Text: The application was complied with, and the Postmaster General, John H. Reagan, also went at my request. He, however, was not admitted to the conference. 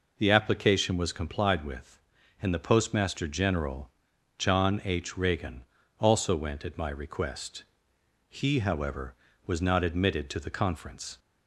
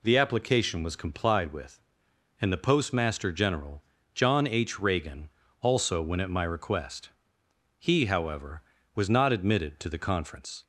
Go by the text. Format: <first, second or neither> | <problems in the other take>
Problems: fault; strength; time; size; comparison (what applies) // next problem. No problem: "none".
neither | none